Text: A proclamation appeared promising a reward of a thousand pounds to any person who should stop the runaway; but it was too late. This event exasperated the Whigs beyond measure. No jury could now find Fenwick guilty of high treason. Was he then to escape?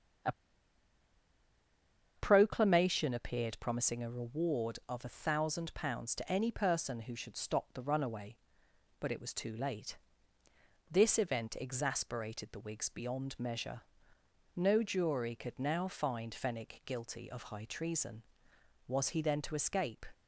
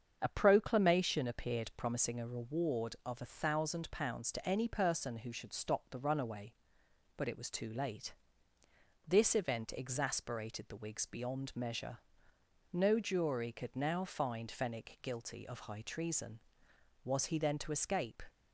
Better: second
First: starts louder than the rest; strong; until 3.1 s; 7.5 dB // pauses between "A" and "proclamation"; strong; at 0.3 s; 1.8 s long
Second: starts louder than the rest; strong; until 1.2 s; 7.5 dB

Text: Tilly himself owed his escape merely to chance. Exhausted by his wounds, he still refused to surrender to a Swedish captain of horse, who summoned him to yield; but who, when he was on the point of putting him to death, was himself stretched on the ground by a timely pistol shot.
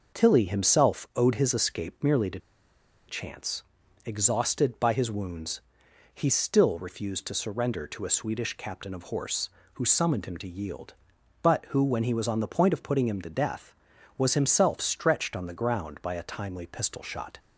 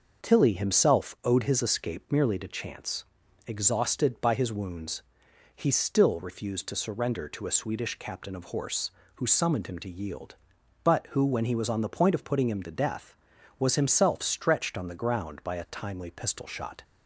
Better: second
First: pauses between "to" and "chance"; noticeable; at 2.3 s; 0.68 s long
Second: none

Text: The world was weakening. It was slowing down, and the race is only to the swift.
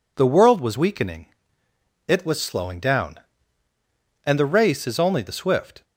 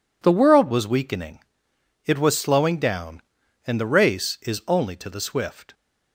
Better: second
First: skips "to"; at 5.2 s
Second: none

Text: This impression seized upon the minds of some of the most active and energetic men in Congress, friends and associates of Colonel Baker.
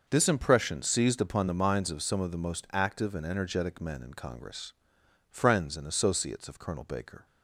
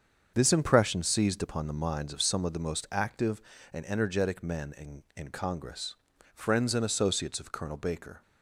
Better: first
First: starts louder than the rest; noticeable; until 1.0 s; 6 dB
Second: starts louder than the rest; until 1.3 s; 7 dB // says "in" twice; at 5.1 s

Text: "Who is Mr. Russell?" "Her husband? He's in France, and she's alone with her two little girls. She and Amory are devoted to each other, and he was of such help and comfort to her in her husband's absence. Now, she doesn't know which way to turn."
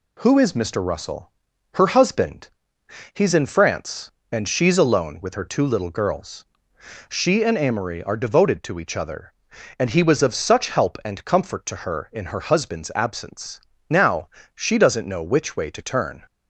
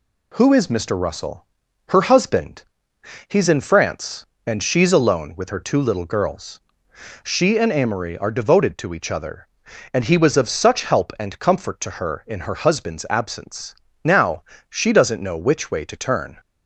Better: neither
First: none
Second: none

